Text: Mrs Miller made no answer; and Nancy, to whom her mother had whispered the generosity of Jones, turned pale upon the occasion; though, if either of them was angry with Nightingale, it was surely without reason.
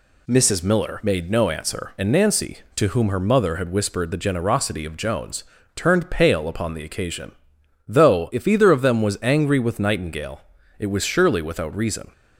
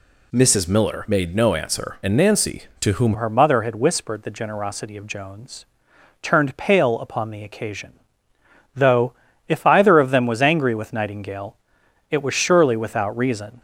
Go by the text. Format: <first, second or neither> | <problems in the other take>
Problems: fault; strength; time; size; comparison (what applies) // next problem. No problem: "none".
first | changes voice at "her"; from 3.1 s on; 10.4 s long